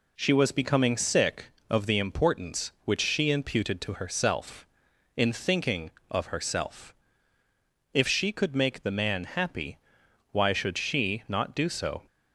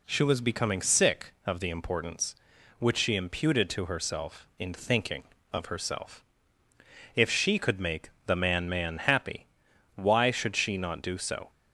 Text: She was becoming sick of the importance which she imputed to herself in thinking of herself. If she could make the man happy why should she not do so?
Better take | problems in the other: first | pauses between "make" and "the"; slight; at 8.0 s; 0.16 s long // says "man" twice; at 8.6 s // pauses between "happy" and "why"; noticeable; at 9.4 s; 0.50 s long; noticeable in the first

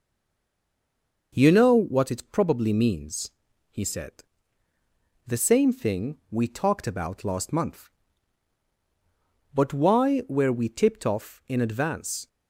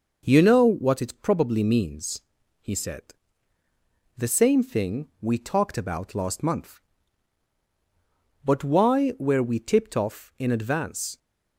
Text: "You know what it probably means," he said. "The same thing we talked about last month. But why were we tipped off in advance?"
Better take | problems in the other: second | stays silent before the first word; noticeable; until 1.3 s; 1.3 s long

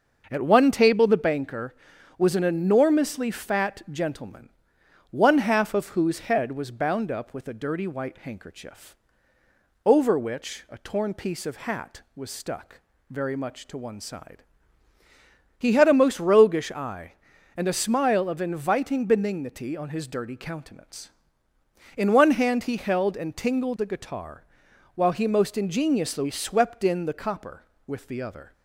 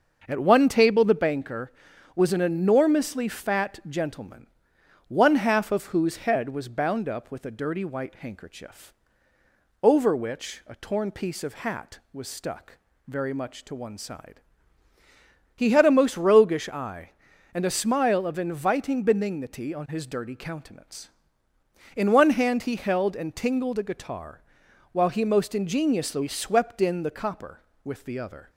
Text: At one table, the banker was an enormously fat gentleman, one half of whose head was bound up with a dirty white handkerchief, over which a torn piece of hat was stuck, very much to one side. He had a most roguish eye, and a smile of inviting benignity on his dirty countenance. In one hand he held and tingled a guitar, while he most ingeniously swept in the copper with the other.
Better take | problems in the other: neither | starts louder than the rest; the same in both

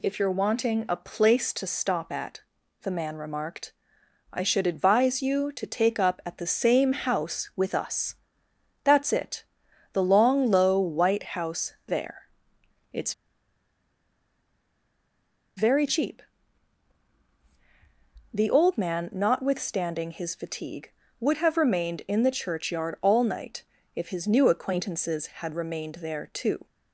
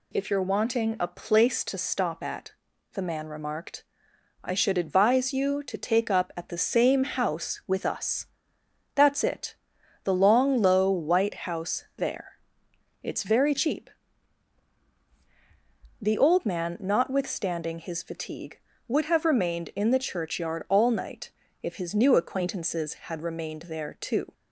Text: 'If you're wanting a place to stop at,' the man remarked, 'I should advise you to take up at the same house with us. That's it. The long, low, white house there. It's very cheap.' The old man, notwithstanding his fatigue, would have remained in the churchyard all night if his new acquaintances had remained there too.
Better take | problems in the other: second | pauses between "It's" and "very"; strong; at 13.1 s; 2.4 s long // pauses between "night" and "if"; slight; at 23.6 s; 0.32 s long; slight in the second

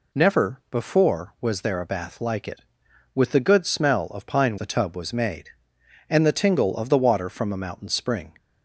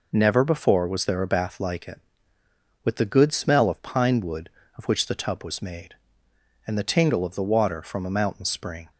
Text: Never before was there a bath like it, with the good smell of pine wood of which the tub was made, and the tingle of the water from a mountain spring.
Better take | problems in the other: second | skips "wood of which"; at 4.5 s

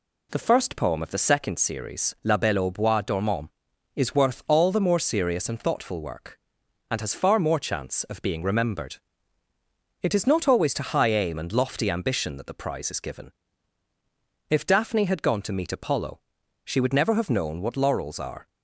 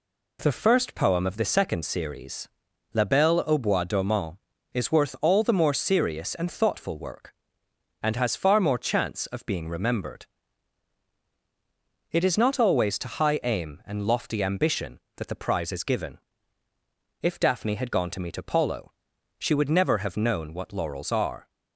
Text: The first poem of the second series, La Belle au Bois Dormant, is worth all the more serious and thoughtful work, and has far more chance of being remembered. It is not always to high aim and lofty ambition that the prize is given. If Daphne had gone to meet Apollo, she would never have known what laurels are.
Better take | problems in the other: neither | none

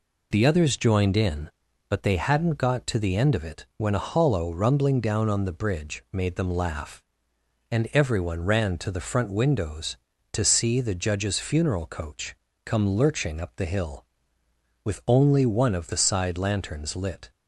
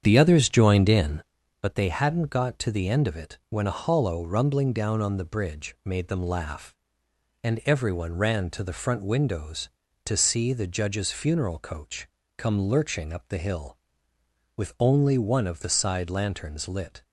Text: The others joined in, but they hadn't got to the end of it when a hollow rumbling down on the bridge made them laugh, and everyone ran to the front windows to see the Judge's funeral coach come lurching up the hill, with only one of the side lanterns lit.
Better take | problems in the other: first | starts louder than the rest; strong; until 1.3 s; 8 dB // pauses between "coach" and "come"; slight; at 12.0 s; 0.30 s long; slight in the first

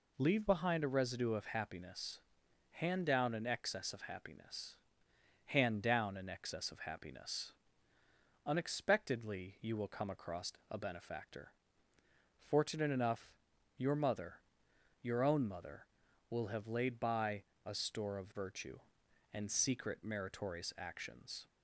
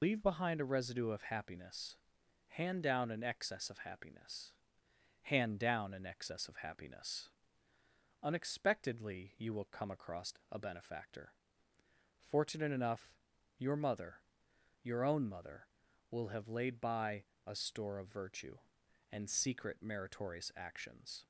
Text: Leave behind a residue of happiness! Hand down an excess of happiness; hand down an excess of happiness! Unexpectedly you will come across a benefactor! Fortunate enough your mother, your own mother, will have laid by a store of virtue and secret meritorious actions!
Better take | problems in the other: first | loses the start of "Leave"; at 0.0 s; 90 ms // pauses between "across" and "a"; slight; at 10.3 s; 0.18 s long; slight in the first // pauses between "enough" and "your"; at 13.1 s; 0.44 s long; also in the first // pauses between "by" and "a"; slight; at 17.2 s; 0.24 s long; slight in the first

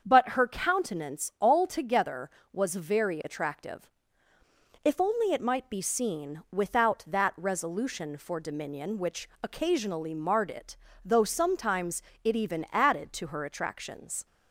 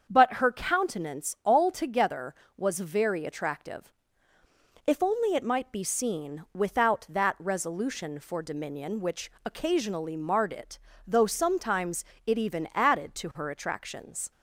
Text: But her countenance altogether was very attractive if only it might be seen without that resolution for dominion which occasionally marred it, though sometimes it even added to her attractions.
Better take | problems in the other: neither | starts louder than the rest; the same in both // pauses between "attractive" and "if"; noticeable; the same in both // pauses between "sometimes" and "it"; slight; the same in both

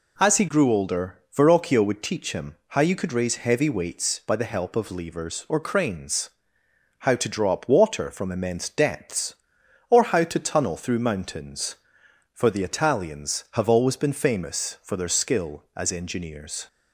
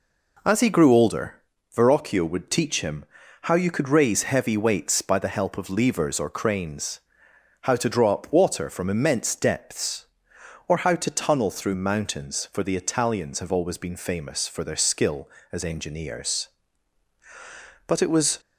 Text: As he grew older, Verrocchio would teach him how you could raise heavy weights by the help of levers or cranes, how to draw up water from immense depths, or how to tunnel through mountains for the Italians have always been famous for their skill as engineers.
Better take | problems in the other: first | pauses between "him" and "how"; slight; at 3.0 s; 0.36 s long // goes on to say "But it was"; from 17.8 s on; 0.54 s long

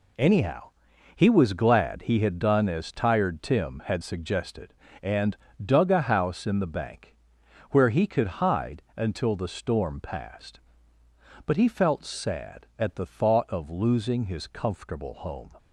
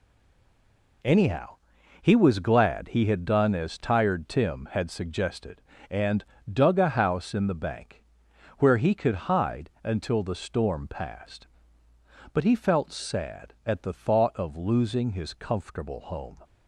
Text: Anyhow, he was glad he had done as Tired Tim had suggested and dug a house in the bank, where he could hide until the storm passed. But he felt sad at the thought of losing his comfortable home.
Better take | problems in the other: first | stays silent before the first word; until 1.0 s; 1.0 s long // pauses between "and" and "dug"; slight; at 6.2 s; 0.28 s long; slight in the first

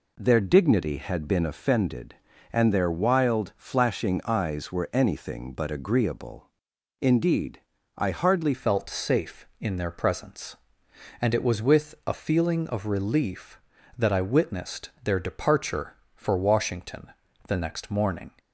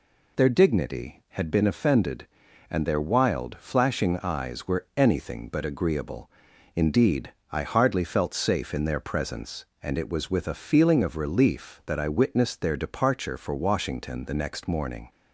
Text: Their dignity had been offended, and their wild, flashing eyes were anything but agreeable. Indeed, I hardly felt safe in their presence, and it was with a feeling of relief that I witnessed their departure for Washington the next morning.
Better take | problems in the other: second | changes voice at "felt"; from 8.5 s on; 9.8 s long // pauses between "Washington" and "the"; at 17.0 s; 0.40 s long

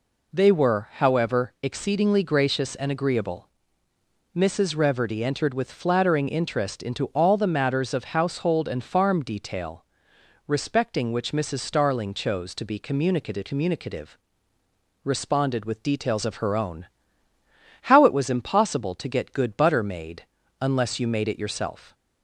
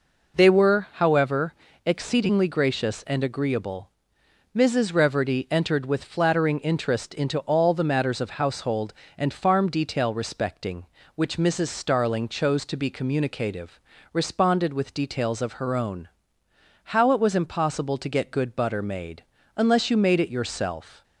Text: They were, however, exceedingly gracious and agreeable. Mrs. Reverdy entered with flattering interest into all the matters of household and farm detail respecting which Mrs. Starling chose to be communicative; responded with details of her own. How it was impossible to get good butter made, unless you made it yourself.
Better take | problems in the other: second | pauses between "detail" and "respecting"; noticeable; at 9.8 s; 0.64 s long // says "communicative" twice; at 13.4 s

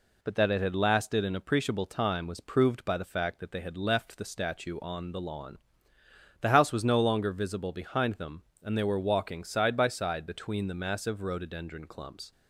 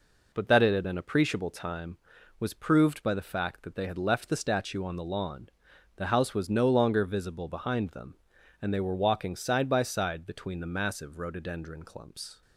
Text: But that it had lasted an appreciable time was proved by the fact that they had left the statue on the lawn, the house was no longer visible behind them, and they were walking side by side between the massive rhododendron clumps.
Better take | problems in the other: first | skips "lasted"; at 0.8 s

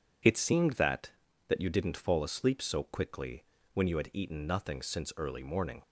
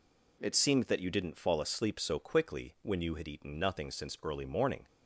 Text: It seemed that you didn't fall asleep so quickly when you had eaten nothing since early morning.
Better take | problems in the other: second | says "that" twice; at 1.4 s // pauses between "quickly" and "when"; slight; at 3.4 s; 0.30 s long

